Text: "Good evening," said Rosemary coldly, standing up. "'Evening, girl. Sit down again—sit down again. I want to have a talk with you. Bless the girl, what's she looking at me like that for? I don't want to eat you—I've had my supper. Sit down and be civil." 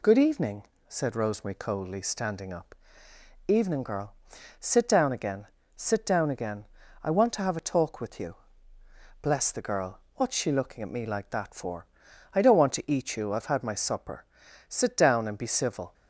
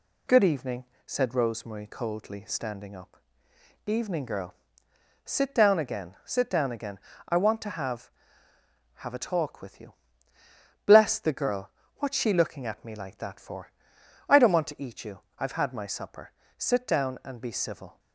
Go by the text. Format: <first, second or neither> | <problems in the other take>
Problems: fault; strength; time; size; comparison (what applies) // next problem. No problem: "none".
first | says "have" twice; at 9.0 s